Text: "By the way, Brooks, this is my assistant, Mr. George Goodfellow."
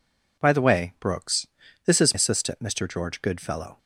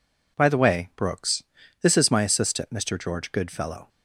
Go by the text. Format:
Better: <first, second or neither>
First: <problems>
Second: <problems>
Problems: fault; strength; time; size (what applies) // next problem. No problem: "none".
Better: second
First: skips "my"; at 2.1 s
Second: none